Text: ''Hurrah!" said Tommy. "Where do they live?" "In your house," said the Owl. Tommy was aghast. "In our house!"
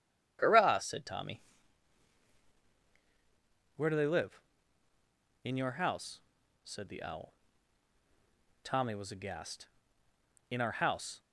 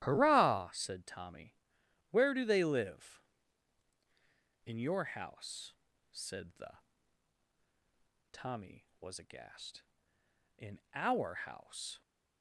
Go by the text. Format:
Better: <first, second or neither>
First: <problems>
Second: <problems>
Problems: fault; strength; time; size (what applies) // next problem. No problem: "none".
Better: first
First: none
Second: starts louder than the rest; strong; until 1.0 s; 13 dB // skips "Owl"; at 7.5 s